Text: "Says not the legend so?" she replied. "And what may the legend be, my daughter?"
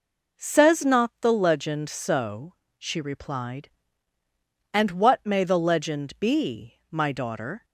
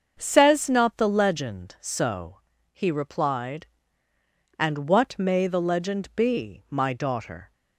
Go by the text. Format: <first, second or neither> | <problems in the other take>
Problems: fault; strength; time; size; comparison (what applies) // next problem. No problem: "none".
first | starts louder than the rest; until 1.2 s; 6.5 dB // says "he" for "she"; at 2.7 s